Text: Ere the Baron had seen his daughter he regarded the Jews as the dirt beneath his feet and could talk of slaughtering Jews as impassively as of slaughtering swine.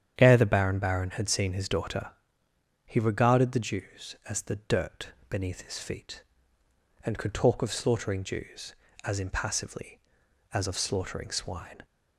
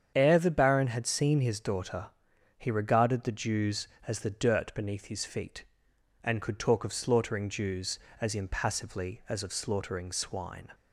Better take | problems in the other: second | starts louder than the rest; strong; until 1.1 s; 9 dB; strong in the second // says "Baron" twice; at 0.7 s // pauses between "daughter" and "he"; noticeable; at 2.1 s; 0.76 s long; noticeable in the second // pauses between "dirt" and "beneath"; slight; at 5.0 s; 0.20 s long

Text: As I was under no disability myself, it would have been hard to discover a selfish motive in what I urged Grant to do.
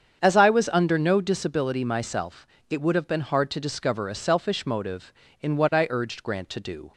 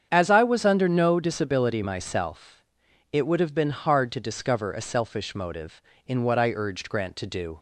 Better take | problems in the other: neither | starts louder than the rest; strong; the same in both

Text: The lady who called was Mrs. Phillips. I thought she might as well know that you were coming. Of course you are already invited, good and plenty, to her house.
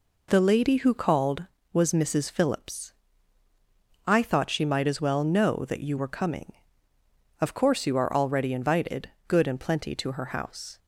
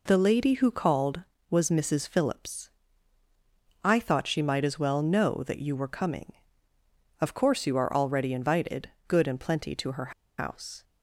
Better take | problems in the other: first | pauses between "her" and "house"; slight; at 10.1 s; 0.26 s long

